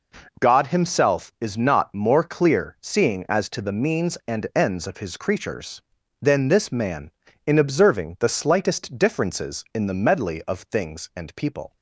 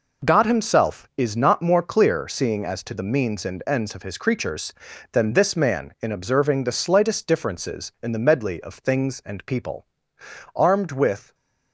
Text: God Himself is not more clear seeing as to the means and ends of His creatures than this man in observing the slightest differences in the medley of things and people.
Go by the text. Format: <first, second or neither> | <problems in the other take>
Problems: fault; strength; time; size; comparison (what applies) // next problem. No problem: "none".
first | goes on to say "Armed with"; noticeable; from 10.5 s on; 0.80 s long